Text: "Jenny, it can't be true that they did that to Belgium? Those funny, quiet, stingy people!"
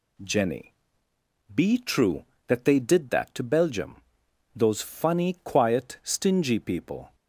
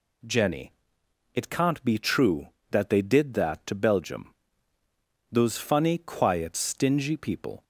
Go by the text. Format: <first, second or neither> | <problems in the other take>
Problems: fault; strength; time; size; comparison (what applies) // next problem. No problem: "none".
second | skips "it can't"; at 1.1 s